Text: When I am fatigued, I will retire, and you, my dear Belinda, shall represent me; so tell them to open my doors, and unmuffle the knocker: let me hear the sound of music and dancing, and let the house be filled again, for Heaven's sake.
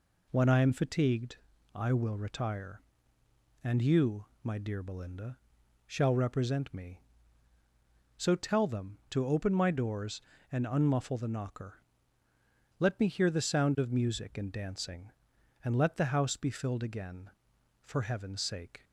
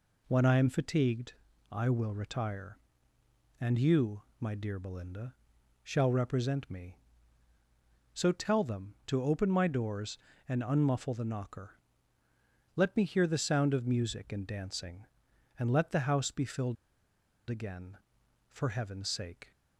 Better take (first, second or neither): first